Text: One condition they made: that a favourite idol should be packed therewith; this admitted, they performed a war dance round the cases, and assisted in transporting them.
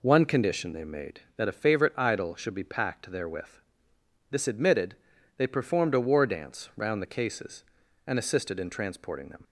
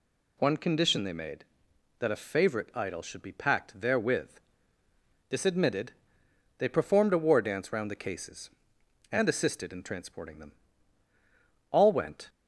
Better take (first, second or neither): first